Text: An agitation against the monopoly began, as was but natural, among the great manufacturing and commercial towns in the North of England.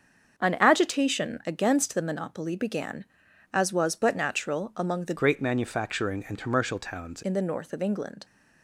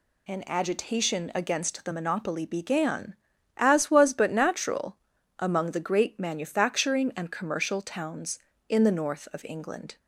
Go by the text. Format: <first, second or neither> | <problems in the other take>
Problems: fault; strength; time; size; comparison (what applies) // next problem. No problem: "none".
second | starts louder than the rest; until 1.5 s; 7 dB // changes voice from "great" to "towns"; from 5.1 to 7.2 s; 2.1 s long